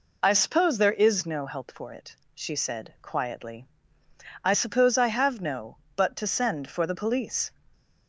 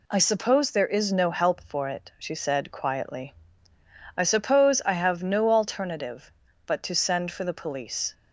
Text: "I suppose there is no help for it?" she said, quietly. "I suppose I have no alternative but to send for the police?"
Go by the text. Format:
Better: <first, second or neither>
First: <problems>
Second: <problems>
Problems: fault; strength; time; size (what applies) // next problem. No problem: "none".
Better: second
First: skips "alternative"; at 5.8 s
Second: none